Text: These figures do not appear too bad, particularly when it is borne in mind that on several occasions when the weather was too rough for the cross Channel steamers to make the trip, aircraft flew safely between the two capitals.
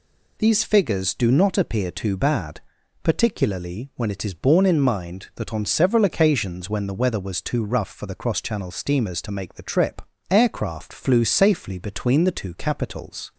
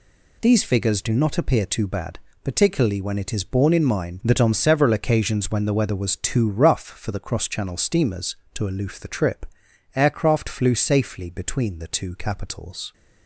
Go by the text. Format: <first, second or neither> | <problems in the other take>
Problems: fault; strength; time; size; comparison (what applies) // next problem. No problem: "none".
first | says "aloof" for "make"; at 8.6 s